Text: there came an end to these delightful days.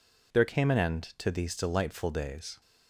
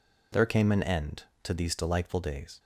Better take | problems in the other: neither | none

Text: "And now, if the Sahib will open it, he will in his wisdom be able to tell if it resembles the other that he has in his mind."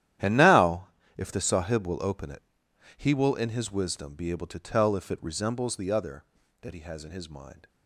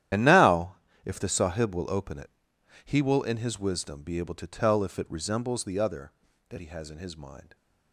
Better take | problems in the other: first | loses the start of "And"; at 0.1 s; 40 ms // starts louder than the rest; strong; until 1.4 s; 11.5 dB; strong in the first

